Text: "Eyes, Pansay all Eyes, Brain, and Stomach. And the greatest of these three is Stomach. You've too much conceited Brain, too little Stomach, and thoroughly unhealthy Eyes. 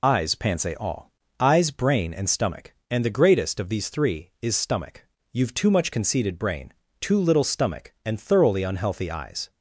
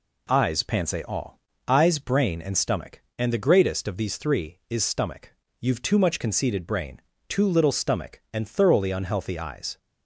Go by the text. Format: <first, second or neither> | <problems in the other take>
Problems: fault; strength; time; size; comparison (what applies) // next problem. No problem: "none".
second | loses the start of "Eyes"; at 0.0 s; 40 ms // pauses between "all" and "Eyes"; slight; at 1.1 s; 0.26 s long; slight in the second